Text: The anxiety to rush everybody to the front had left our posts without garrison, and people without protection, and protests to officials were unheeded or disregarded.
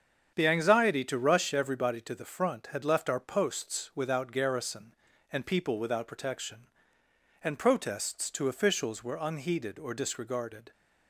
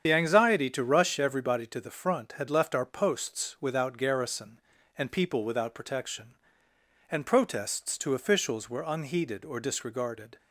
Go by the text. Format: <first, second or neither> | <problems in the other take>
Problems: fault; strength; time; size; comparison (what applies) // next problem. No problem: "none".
first | loses the start of "The"; at 0.0 s; 45 ms // starts louder than the rest; strong; until 1.0 s; 8 dB; strong in the first